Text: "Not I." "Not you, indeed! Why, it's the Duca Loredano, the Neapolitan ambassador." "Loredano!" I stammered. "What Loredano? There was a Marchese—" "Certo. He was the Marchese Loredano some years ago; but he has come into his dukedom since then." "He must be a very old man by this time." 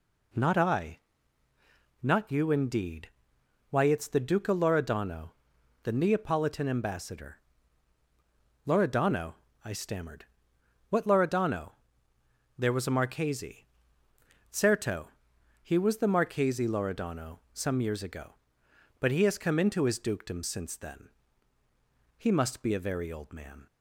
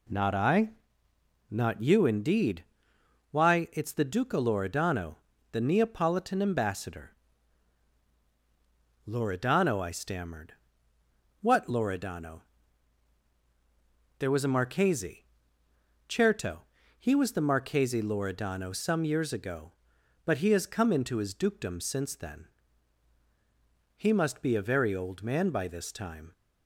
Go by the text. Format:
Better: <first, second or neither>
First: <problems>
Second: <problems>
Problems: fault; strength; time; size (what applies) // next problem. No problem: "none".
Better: second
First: stops before "by this time"; at 23.6 s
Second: none